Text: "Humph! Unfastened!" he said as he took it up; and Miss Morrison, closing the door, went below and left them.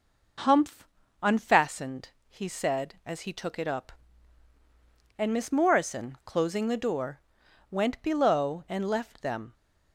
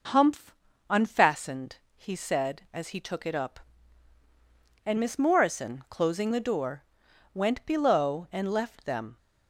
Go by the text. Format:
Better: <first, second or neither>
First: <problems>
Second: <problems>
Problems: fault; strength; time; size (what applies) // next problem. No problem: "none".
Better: neither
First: none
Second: none